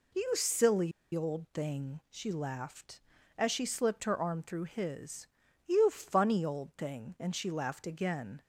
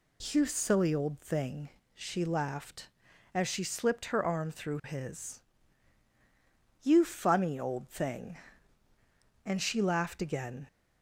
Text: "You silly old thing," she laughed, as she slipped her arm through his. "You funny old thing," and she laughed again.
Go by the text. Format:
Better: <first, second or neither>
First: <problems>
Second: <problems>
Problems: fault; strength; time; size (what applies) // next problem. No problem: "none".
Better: second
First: pauses between "silly" and "old"; slight; at 0.9 s; 0.23 s long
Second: none